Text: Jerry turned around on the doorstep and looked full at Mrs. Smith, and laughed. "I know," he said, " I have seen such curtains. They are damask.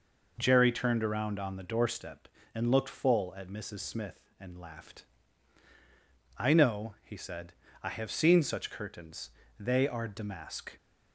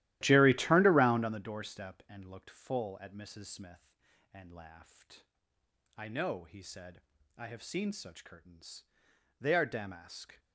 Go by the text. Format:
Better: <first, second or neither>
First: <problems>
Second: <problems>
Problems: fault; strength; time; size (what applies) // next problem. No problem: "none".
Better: first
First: none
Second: starts louder than the rest; strong; until 1.4 s; 14.5 dB